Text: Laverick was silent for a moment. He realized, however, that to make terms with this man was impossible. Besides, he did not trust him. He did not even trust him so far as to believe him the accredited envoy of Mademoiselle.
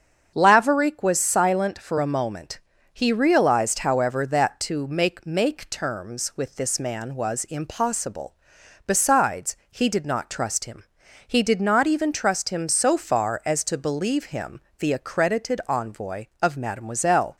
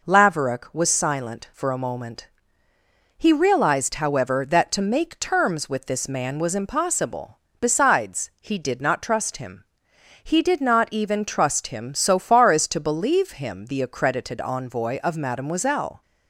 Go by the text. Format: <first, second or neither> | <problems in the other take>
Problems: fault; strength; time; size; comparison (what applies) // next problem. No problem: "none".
second | starts louder than the rest; until 1.3 s; 7 dB // says "make" twice; at 5.2 s // pauses between "him" and "the"; slight; at 14.5 s; 0.18 s long